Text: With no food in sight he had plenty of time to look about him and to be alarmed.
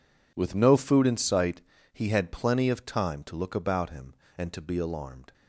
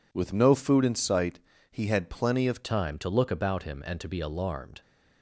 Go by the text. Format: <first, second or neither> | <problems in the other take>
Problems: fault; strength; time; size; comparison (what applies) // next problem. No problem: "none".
first | pauses between "sight" and "he"; slight; at 1.3 s; 0.32 s long; slight in the first // changes voice at "time"; from 2.6 s on; 2.2 s long